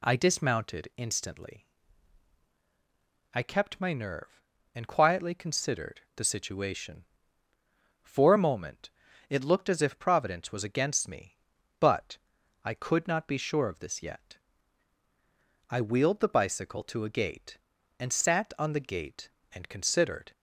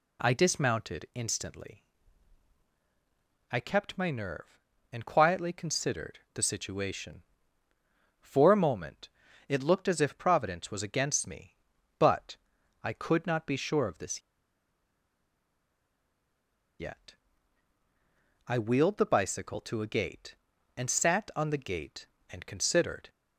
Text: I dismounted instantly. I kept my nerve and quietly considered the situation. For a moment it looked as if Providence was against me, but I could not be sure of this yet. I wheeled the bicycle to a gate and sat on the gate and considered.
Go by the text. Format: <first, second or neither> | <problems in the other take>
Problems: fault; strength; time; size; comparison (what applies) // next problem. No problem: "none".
first | pauses between "considered" and "the"; slight; at 6.1 s; 0.16 s long; slight in the first // pauses between "moment" and "it"; at 9.0 s; 0.40 s long; also in the first // pauses between "but" and "I"; noticeable; at 12.3 s; 0.46 s long; noticeable in the first // pauses between "this" and "yet"; strong; at 14.2 s; 2.5 s long